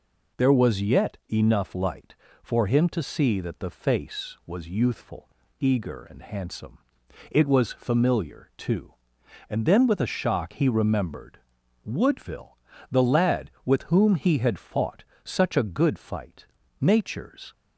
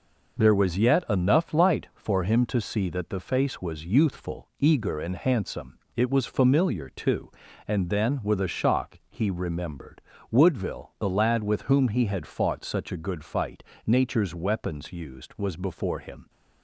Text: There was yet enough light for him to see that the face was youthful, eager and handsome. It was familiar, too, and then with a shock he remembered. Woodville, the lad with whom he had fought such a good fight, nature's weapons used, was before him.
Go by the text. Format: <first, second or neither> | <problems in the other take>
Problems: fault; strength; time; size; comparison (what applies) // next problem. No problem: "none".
second | pauses between "fought" and "such"; slight; at 15.0 s; 0.18 s long // stops before "weapons used was before him"; at 17.5 s